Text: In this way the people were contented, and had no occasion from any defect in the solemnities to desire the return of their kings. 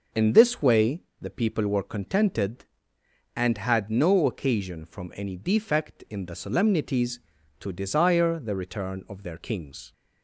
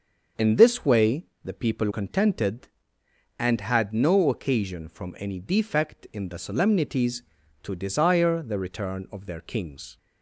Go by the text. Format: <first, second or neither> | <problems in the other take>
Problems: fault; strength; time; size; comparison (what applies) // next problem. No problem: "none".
first | starts louder than the rest; until 1.5 s; 6.5 dB // pauses between "way" and "the"; slight; at 1.2 s; 0.18 s long; slight in the first // skips "were"; at 1.9 s